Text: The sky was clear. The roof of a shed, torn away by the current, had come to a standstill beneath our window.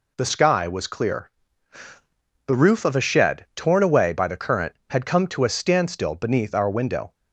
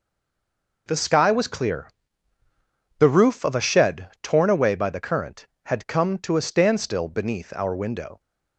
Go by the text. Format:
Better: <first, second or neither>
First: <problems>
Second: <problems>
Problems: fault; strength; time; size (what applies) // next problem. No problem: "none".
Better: first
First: none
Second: stays silent before the first word; slight; until 0.8 s; 0.8 s long